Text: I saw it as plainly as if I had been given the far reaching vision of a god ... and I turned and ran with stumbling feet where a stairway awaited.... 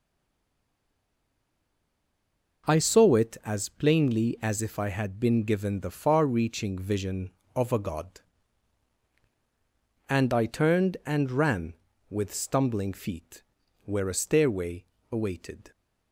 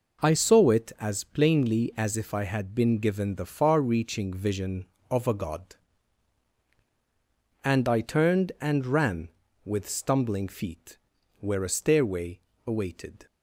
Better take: second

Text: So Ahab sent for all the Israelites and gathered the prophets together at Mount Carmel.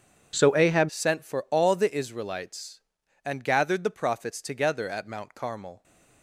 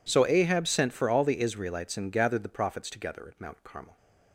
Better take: second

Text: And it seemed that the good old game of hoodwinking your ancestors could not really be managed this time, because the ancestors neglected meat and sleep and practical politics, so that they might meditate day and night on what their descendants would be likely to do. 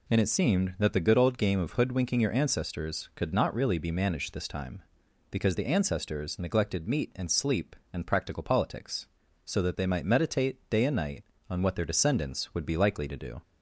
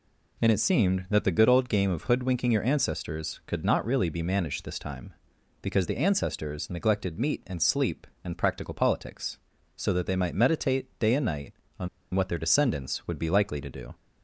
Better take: first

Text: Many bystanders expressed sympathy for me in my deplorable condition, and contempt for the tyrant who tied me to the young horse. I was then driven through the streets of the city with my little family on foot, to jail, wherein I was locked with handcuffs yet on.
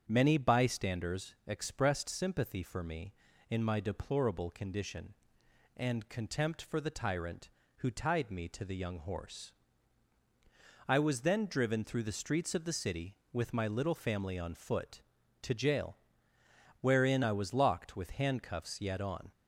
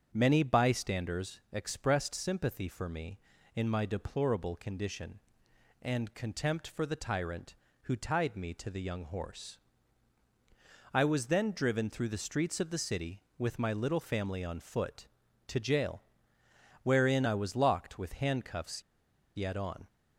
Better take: first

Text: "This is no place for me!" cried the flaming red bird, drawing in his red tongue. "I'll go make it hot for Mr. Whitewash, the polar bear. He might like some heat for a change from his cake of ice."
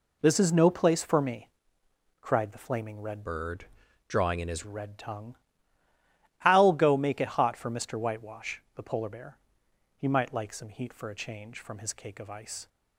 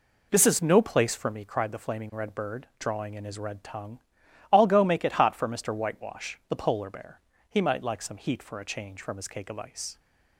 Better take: second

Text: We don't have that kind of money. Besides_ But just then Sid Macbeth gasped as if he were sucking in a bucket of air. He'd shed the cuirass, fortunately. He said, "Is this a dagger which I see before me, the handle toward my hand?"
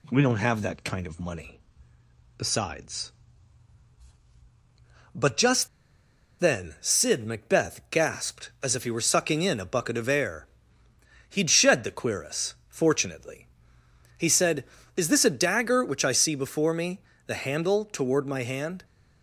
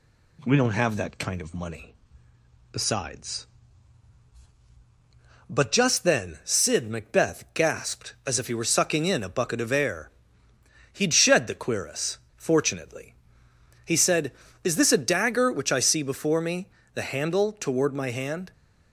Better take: second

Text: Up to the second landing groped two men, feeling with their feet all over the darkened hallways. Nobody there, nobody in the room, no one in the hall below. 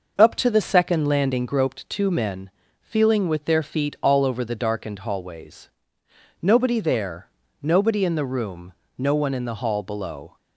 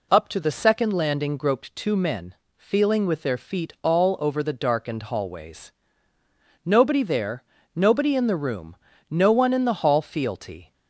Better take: first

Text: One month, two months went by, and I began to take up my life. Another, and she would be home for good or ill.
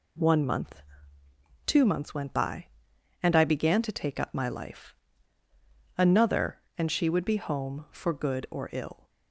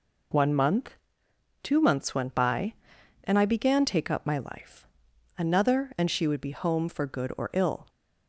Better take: first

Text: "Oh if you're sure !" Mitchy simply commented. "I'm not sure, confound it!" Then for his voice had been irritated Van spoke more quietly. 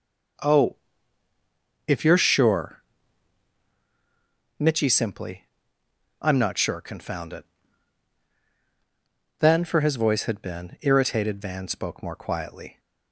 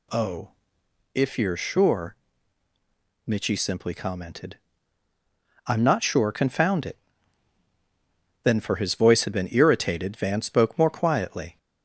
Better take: second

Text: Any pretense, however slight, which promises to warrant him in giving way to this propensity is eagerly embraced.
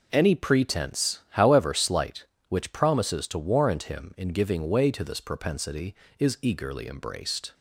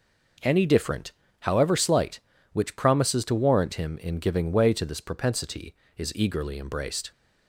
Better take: first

